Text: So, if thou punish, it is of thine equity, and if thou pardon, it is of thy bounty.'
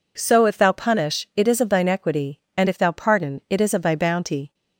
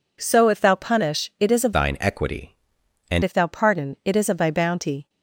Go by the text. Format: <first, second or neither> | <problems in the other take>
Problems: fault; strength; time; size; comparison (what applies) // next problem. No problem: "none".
first | changes voice from "thine" to "and"; from 1.7 to 3.2 s; 1.5 s long